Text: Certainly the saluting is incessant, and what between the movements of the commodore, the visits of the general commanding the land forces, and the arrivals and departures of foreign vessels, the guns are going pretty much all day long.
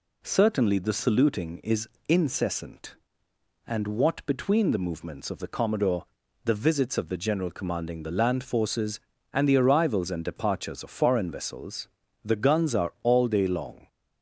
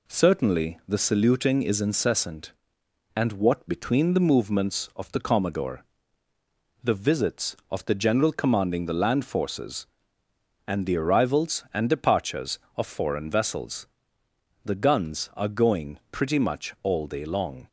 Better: second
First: pauses between "is" and "incessant"; slight; at 1.8 s; 0.20 s long // skips "going pretty much"; at 12.9 s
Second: none

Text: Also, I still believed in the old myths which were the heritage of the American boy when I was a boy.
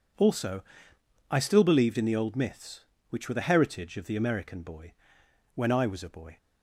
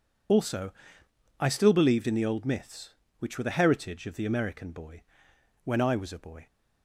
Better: first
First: pauses between "boy" and "when"; noticeable; at 4.9 s; 0.62 s long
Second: loses the start of "Also"; at 0.2 s; 40 ms // pauses between "boy" and "when"; noticeable; at 5.0 s; 0.62 s long

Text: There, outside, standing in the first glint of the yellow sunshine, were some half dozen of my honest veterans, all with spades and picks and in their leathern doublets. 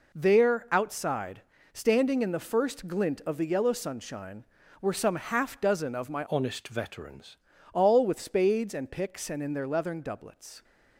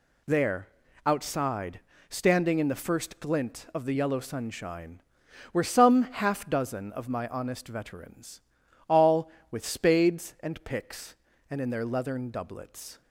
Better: second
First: changes voice from "honest" to "veterans"; from 6.2 to 7.3 s; 1.1 s long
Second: none

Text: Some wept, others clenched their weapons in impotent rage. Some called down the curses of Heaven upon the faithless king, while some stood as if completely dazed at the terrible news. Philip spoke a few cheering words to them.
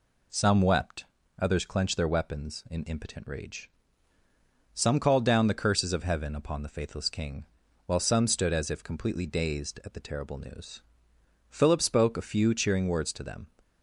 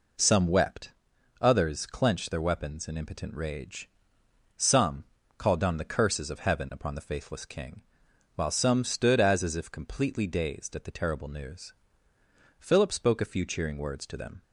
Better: first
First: none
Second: pauses between "Some" and "called"; slight; at 5.0 s; 0.32 s long // says "as" twice; at 9.4 s

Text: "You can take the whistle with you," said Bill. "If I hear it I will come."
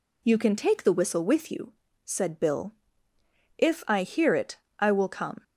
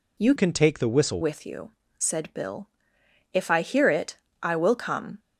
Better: first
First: pauses between "it" and "I"; slight; at 4.5 s; 0.20 s long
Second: changes voice from "can" to "whistle"; from 0.3 to 1.1 s; 0.8 s long // pauses between "it" and "I"; slight; at 4.1 s; 0.24 s long

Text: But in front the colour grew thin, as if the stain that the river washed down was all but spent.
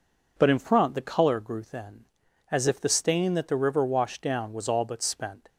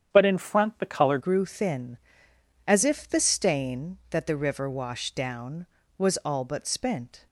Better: first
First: none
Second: starts louder than the rest; strong; until 1.1 s; 9 dB // changes voice at "grew"; from 1.1 s on; 6.1 s long

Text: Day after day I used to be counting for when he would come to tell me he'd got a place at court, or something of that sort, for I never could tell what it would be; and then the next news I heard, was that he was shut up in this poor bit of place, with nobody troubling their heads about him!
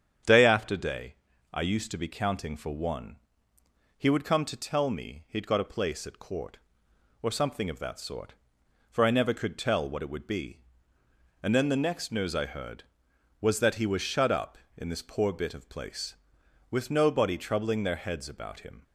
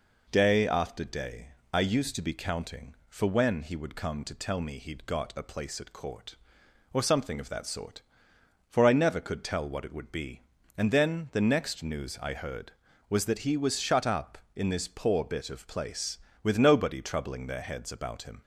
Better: second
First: starts louder than the rest; strong; until 1.6 s; 8.5 dB // pauses between "day" and "I"; at 1.1 s; 0.38 s long // says "one" for "when"; at 2.7 s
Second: pauses between "day" and "I"; slight; at 1.5 s; 0.20 s long

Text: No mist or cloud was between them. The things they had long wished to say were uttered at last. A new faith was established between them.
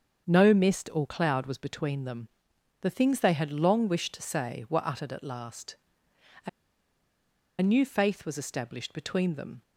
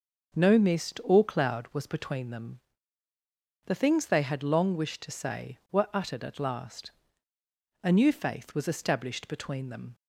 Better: second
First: starts louder than the rest; until 1.2 s; 7 dB // pauses between "A" and "new"; at 6.4 s; 1.1 s long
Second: none

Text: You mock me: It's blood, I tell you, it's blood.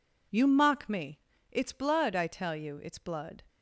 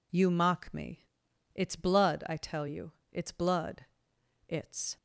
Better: first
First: none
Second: goes on to say "It's"; from 4.4 s on; 0.50 s long

